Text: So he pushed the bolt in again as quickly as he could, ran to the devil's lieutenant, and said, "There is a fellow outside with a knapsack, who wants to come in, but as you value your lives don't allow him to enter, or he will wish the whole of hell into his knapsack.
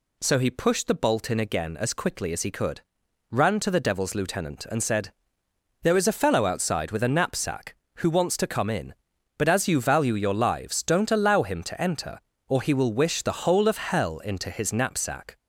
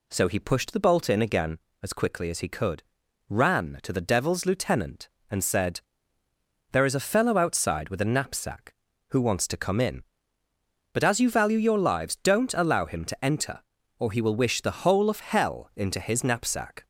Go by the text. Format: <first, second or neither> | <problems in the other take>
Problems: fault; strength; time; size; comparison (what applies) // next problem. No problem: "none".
neither | none